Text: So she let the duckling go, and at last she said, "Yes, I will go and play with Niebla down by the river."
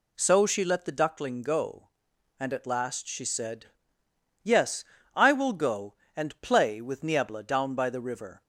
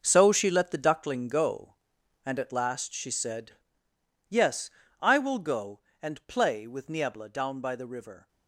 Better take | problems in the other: first | gets quieter; strong; throughout; 11.5 dB

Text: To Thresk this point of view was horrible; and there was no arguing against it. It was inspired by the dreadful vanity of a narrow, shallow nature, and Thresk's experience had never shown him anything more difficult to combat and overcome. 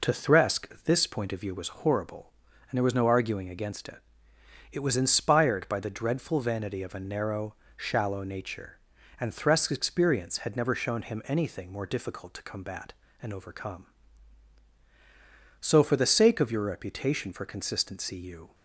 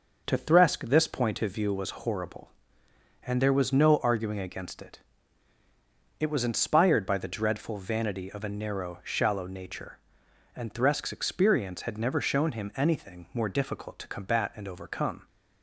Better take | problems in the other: second | goes on to say "So for the sake of your reputation for consistency you"; strong; from 15.6 s on; 2.9 s long

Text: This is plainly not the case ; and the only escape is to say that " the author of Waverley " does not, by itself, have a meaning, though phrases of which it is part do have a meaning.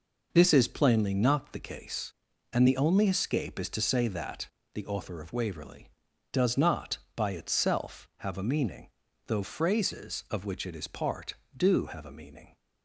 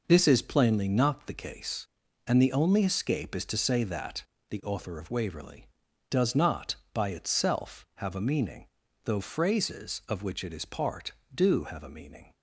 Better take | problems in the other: neither | none

